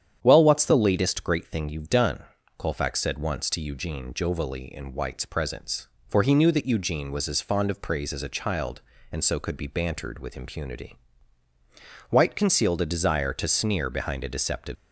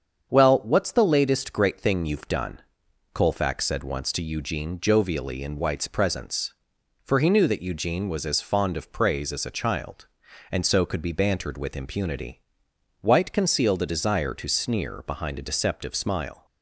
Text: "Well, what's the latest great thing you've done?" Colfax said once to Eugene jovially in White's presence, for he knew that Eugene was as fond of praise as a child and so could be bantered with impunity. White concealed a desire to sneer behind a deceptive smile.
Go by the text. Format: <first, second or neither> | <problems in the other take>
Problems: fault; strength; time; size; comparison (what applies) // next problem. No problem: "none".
second | starts louder than the rest; strong; until 1.2 s; 9 dB; strong in the second // stops before "smile"; at 14.7 s